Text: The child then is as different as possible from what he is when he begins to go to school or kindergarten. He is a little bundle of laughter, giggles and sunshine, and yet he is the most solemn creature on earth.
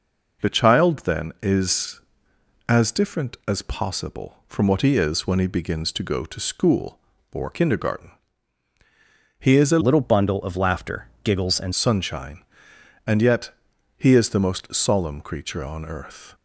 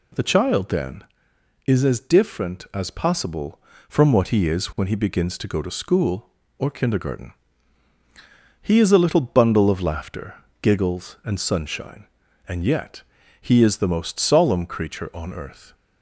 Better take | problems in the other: second | changes voice from "little" to "and"; from 9.8 to 11.7 s; 1.9 s long // pauses between "yet" and "he"; noticeable; at 13.5 s; 0.46 s long; also in the second

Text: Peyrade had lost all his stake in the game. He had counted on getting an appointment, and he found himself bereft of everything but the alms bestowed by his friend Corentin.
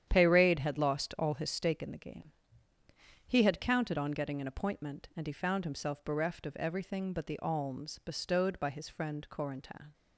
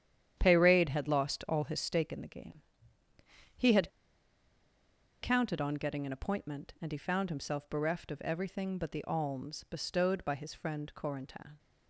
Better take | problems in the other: first | starts louder than the rest; strong; until 1.3 s; 9.5 dB; strong in the first // pauses between "had" and "counted"; strong; at 3.8 s; 1.3 s long

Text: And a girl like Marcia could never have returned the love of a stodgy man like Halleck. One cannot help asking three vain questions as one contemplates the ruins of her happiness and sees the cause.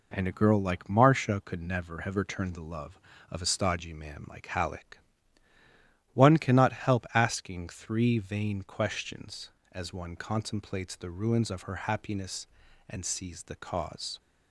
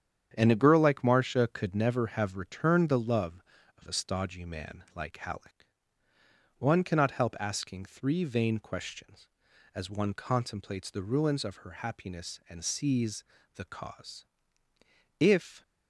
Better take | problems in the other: first | starts louder than the rest; strong; until 1.3 s; 9 dB // pauses between "sees" and "the"; slight; at 13.2 s; 0.32 s long // goes on to say "If"; slight; from 15.2 s on; 0.42 s long

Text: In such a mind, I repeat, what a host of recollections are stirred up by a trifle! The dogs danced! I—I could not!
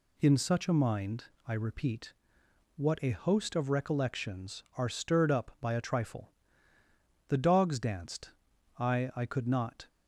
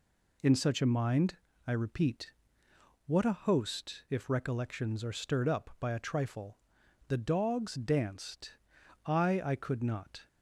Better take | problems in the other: first | says "if" for "of"; at 4.0 s

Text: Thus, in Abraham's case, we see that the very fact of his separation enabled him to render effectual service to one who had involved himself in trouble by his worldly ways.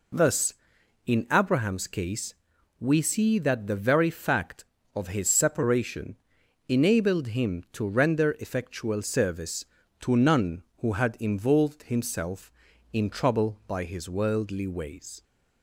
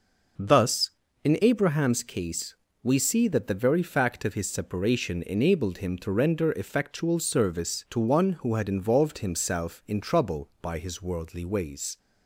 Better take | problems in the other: second | pauses between "separation" and "enabled"; noticeable; at 6.1 s; 0.50 s long // says "none" for "one"; at 10.1 s

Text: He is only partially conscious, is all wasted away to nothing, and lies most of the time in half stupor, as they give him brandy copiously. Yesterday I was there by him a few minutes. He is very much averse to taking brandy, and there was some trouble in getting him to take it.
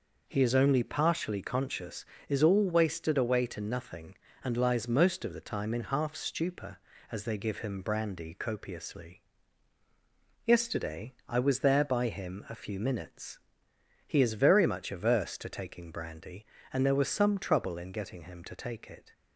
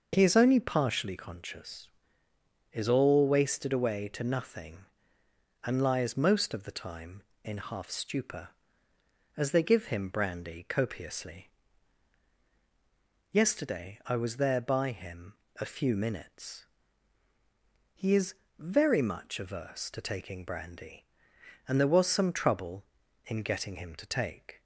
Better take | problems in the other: first | pauses between "him" and "a"; slight; at 15.3 s; 0.24 s long // pauses between "is" and "very"; slight; at 18.3 s; 0.24 s long // stops before "it"; at 24.5 s

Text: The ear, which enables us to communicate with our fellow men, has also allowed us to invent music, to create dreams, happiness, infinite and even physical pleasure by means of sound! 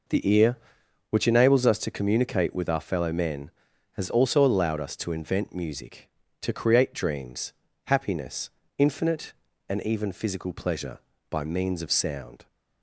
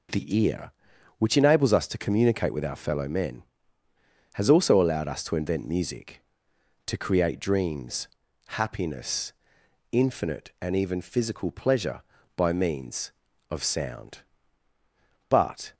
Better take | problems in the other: first | goes on to say "But"; slight; from 15.2 s on; 0.46 s long

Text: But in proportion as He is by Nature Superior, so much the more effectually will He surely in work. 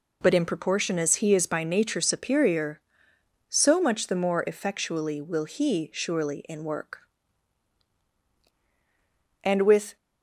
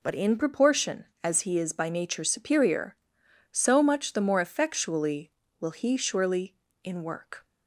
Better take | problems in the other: second | goes on to say "And with"; from 9.4 s on; 0.52 s long

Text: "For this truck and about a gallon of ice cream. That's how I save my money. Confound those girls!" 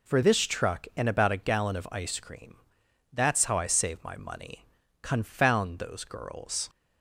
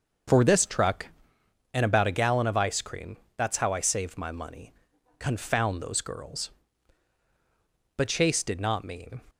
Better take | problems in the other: first | starts louder than the rest; until 1.9 s; 6.5 dB // goes on to say "But Chase did not mean"; noticeable; from 7.9 s on; 1.2 s long

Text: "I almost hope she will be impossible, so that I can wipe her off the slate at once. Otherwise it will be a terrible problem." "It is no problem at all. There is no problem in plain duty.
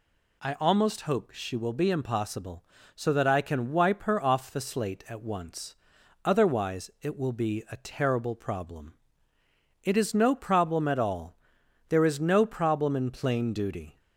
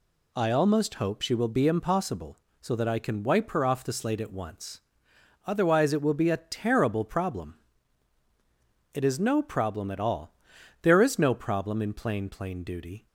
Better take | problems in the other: first | says "plain" twice; at 12.2 s

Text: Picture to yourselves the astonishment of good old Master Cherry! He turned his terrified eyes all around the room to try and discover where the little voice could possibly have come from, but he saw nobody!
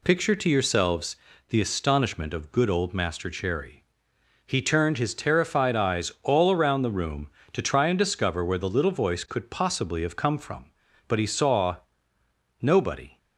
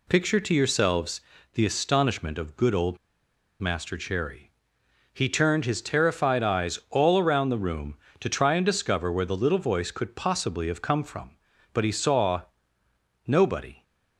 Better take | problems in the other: first | pauses between "yourselves" and "the"; slight; at 1.2 s; 0.32 s long; slight in the first // pauses between "old" and "Master"; noticeable; at 2.9 s; 0.63 s long // pauses between "saw" and "nobody"; noticeable; at 12.4 s; 0.84 s long; noticeable in the first

